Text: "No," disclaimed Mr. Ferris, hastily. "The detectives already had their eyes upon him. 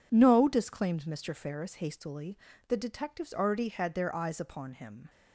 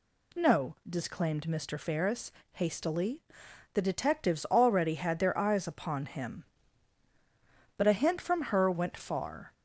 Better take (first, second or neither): first